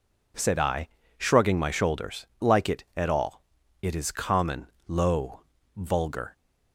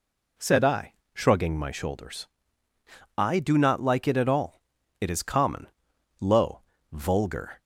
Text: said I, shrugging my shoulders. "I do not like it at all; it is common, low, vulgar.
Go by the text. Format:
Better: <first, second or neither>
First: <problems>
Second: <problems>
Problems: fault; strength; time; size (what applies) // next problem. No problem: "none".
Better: second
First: skips "I do not"; at 2.3 s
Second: none